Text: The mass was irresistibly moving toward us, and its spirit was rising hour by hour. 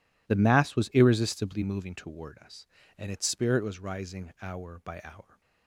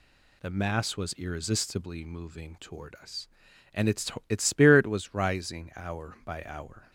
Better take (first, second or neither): first